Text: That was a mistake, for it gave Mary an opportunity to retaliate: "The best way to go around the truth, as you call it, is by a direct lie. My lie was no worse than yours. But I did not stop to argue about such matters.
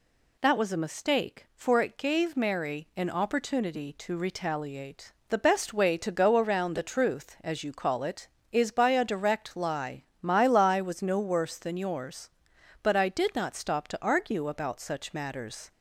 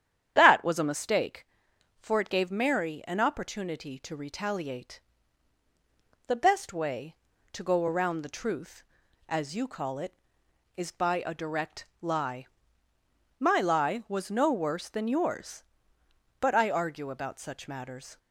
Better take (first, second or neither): first